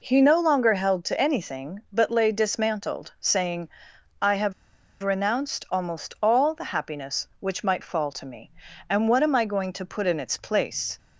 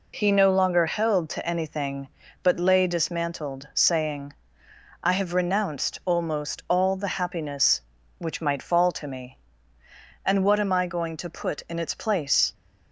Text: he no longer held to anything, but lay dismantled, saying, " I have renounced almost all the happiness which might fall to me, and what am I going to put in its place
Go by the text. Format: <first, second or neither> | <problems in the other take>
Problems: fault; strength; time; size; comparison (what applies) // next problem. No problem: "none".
second | pauses between "have" and "renounced"; noticeable; at 4.5 s; 0.50 s long